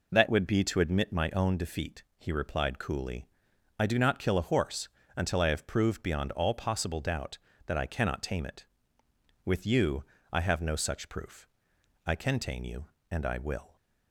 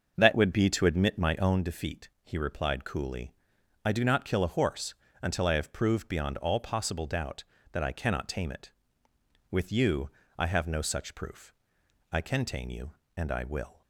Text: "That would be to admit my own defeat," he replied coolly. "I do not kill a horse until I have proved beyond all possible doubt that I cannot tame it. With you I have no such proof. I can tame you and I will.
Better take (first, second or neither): first